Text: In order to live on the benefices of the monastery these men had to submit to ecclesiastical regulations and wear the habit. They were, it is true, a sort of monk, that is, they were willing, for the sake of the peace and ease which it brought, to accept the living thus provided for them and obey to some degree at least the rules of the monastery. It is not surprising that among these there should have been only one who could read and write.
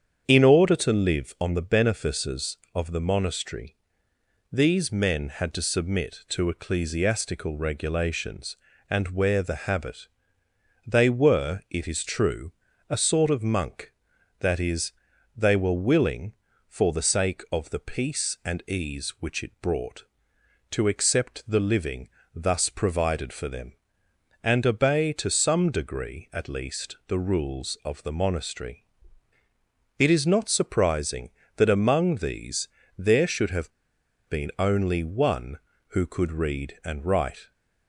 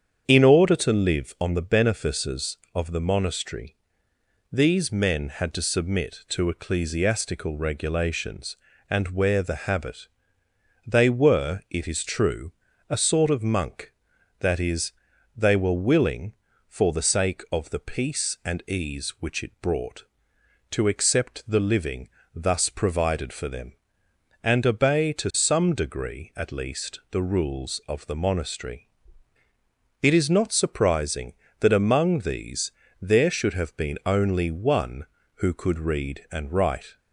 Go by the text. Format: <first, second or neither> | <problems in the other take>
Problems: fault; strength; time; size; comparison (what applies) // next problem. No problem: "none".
second | starts louder than the rest; strong; until 1.2 s; 8 dB; strong in the second // pauses between "monastery" and "these"; noticeable; at 3.7 s; 0.76 s long; noticeable in the second // pauses between "living" and "thus"; slight; at 22.0 s; 0.26 s long; slight in the second // pauses between "these" and "there"; slight; at 32.6 s; 0.30 s long; slight in the second // pauses between "have" and "been"; noticeable; at 33.7 s; 0.58 s long